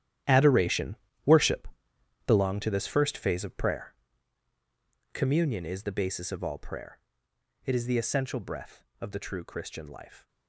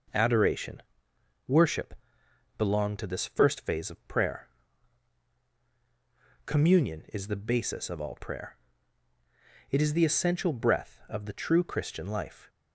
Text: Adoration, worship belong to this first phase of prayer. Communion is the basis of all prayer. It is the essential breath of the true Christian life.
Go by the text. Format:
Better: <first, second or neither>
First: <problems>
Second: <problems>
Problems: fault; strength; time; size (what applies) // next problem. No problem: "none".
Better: second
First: gets quieter; strong; throughout; 14 dB // pauses between "worship" and "belong"; noticeable; at 1.6 s; 0.60 s long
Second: pauses between "worship" and "belong"; noticeable; at 1.9 s; 0.64 s long